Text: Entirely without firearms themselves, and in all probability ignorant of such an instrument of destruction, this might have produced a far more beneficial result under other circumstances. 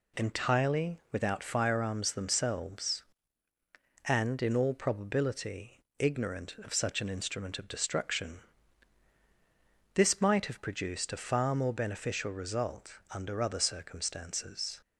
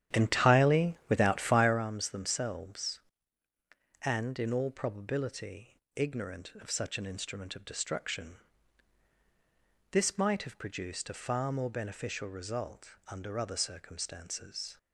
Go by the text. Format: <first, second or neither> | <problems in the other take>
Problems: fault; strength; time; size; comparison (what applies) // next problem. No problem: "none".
first | starts louder than the rest; strong; until 1.9 s; 10.5 dB // pauses between "probability" and "ignorant"; slight; at 5.7 s; 0.18 s long; slight in the first